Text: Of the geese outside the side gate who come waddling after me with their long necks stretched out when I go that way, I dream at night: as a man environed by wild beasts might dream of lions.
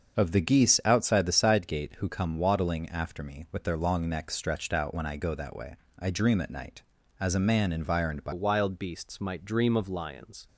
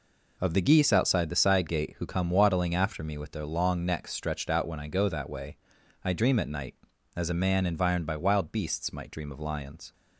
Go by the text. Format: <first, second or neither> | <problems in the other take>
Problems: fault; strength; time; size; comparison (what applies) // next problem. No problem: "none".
second | starts louder than the rest; until 1.1 s; 6.5 dB // changes voice at "wild"; from 8.3 s on; 2.1 s long